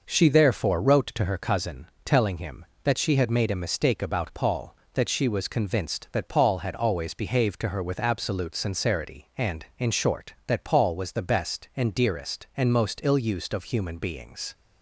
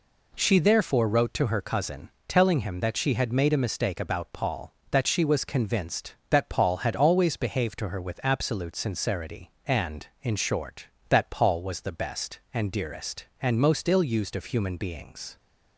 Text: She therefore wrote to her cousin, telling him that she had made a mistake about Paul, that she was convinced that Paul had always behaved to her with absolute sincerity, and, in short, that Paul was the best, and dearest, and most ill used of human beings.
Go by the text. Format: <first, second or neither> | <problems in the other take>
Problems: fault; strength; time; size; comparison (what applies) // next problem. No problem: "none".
neither | none